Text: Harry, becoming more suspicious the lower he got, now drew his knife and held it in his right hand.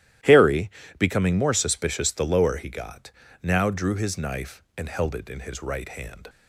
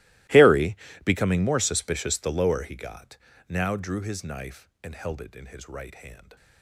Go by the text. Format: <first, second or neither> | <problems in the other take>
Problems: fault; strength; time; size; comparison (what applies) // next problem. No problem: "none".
first | gets quieter; strong; throughout; 22.5 dB // starts louder than the rest; strong; until 1.5 s; 19 dB; strong in the first